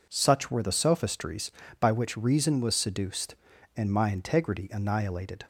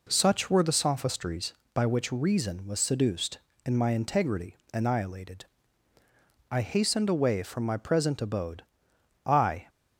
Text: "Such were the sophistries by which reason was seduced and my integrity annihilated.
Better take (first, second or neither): first